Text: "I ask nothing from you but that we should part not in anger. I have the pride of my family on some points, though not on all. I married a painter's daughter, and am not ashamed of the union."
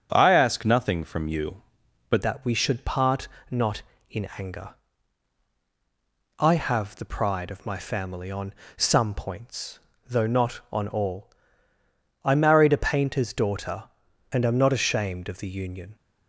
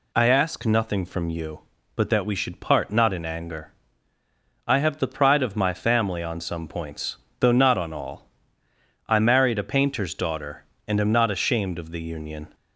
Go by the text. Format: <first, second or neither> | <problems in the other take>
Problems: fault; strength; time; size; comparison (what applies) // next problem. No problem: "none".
second | starts louder than the rest; strong; until 1.1 s; 7.5 dB // changes voice at "that"; from 2.2 s on; 13.7 s long // pauses between "part" and "not"; slight; at 3.2 s; 0.22 s long // pauses between "on" and "some"; slight; at 8.5 s; 0.24 s long